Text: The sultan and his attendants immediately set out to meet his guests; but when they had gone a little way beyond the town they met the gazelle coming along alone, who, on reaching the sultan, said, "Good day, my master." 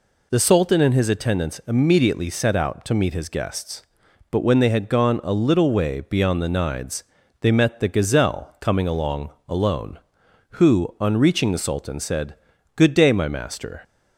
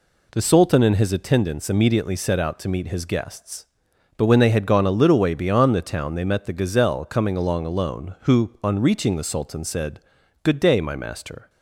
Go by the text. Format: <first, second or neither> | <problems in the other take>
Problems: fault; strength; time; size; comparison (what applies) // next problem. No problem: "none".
second | says "nides" for "town"; at 6.4 s // pauses between "along" and "alone"; slight; at 9.2 s; 0.18 s long